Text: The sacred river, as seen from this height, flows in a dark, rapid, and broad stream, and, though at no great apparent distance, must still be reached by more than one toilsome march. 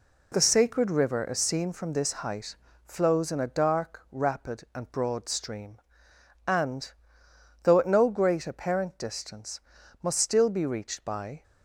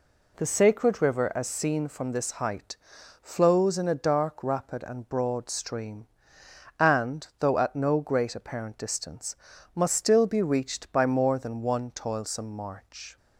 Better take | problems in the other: second | stops before "more than one toilsome march"; at 11.4 s

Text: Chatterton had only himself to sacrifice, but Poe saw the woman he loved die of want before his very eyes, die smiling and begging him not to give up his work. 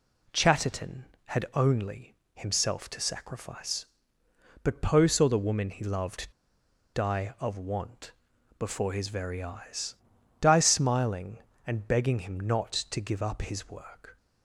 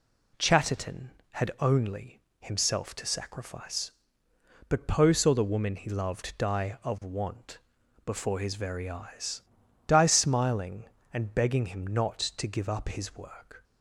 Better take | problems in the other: second | pauses between "only" and "himself"; slight; at 2.1 s; 0.20 s long; slight in the second // pauses between "loved" and "die"; noticeable; at 6.3 s; 0.63 s long // pauses between "want" and "before"; noticeable; at 8.1 s; 0.48 s long; noticeable in the second

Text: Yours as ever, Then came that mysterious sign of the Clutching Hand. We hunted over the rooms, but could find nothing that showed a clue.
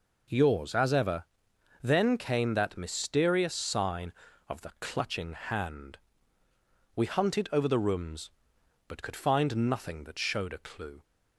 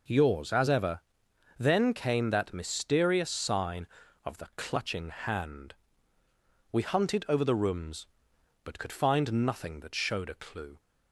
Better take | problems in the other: neither | none

